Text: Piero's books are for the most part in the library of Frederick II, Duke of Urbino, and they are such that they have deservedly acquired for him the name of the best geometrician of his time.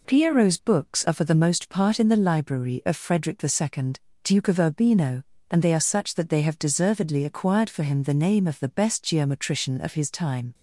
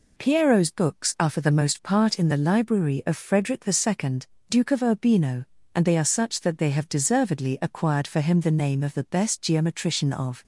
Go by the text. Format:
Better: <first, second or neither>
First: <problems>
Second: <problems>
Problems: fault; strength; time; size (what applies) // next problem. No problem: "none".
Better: first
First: none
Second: stops before "his time"; at 10.4 s